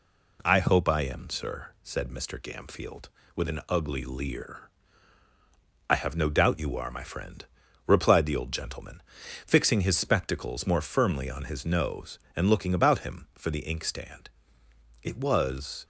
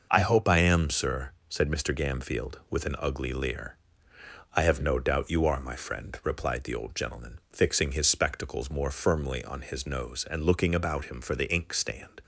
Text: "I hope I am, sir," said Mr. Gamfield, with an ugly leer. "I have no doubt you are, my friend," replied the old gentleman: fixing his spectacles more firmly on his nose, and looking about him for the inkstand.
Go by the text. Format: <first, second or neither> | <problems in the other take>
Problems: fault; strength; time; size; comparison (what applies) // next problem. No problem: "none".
second | goes on to say "It was"; noticeable; from 15.0 s on; 0.82 s long